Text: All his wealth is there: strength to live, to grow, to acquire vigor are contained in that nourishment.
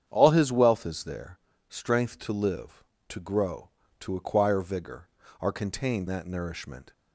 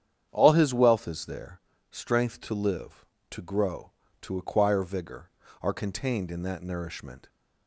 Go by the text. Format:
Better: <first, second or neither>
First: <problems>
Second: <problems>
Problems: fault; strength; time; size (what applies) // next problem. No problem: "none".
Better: second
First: starts louder than the rest; strong; until 1.0 s; 8.5 dB // skips "in"; at 6.0 s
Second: starts louder than the rest; strong; until 1.3 s; 9 dB